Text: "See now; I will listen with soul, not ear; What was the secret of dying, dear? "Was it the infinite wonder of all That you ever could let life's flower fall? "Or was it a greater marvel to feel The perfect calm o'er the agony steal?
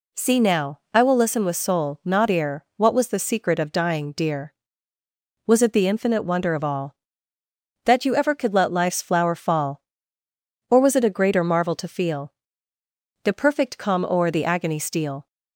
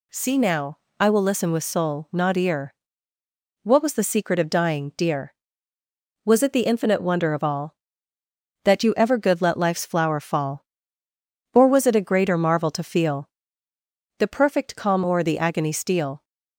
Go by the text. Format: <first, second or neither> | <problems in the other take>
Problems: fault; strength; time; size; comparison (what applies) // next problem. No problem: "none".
first | says "good" for "could"; at 9.1 s // pauses between "feel" and "The"; noticeable; at 13.2 s; 0.90 s long; noticeable in the first